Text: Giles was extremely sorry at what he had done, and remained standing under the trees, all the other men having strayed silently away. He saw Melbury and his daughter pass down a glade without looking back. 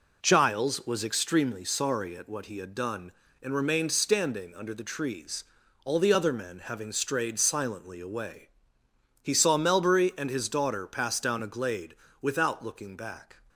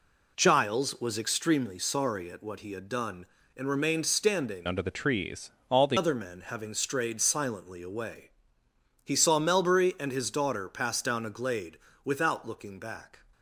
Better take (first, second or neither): first